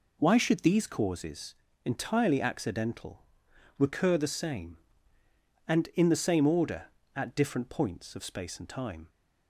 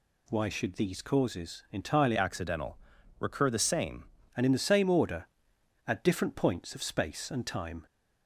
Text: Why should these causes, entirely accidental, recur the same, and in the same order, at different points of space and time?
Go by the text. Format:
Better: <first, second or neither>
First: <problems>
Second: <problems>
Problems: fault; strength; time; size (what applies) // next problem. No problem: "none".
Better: first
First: none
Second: changes voice from "accidental" to "same"; from 2.1 to 4.0 s; 1.9 s long